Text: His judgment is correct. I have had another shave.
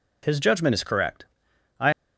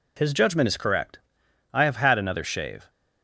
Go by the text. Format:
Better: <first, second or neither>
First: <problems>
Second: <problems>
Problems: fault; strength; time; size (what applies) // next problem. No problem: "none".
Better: second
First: stops before "have had another shave"; at 1.9 s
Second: none